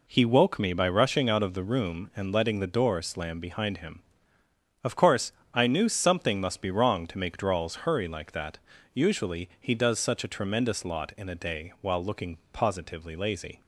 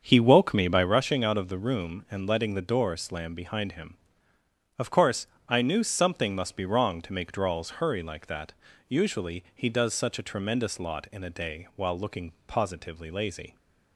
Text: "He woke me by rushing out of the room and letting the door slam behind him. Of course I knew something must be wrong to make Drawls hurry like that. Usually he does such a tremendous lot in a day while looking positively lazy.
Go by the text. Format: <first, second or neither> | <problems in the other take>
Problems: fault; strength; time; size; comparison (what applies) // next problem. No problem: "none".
first | starts louder than the rest; strong; until 0.9 s; 7 dB // pauses between "course" and "I"; slight; at 5.2 s; 0.20 s long; slight in the first // pauses between "looking" and "positively"; slight; at 12.3 s; 0.16 s long; slight in the first